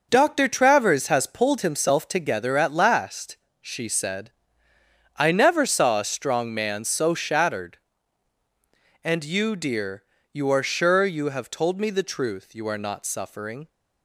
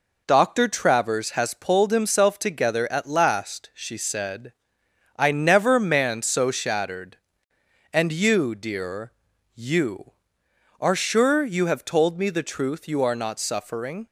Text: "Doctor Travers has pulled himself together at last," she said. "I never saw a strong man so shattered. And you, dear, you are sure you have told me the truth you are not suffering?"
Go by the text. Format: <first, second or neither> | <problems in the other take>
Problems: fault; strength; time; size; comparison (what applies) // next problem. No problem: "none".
first | skips "saw a strong"; at 5.7 s